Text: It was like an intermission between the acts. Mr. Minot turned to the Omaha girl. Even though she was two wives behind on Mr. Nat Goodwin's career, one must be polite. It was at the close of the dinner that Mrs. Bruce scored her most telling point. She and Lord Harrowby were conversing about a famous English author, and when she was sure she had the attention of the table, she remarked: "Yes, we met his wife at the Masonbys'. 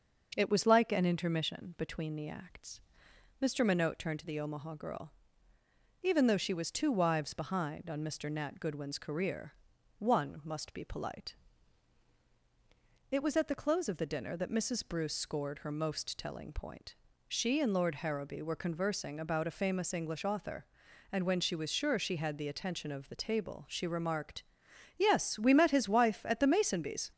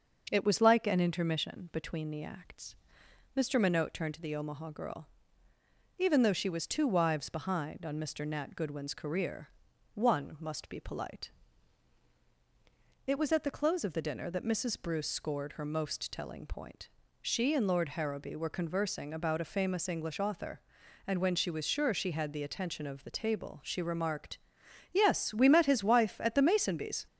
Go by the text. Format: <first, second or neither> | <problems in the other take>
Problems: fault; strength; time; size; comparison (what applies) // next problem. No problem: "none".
neither | starts louder than the rest; the same in both